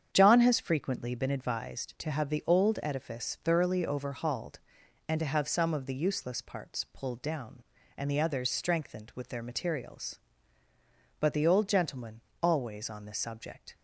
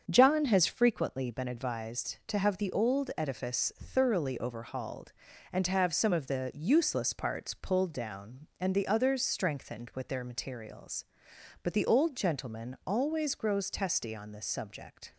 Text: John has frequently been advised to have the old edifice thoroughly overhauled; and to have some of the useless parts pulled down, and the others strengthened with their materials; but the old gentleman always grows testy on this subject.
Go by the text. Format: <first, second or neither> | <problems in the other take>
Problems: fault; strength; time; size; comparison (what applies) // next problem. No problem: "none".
second | starts louder than the rest; strong; until 1.1 s; 8 dB; strong in the second // pauses between "gentleman" and "always"; slight; at 12.2 s; 0.19 s long // skips "grows testy"; at 12.8 s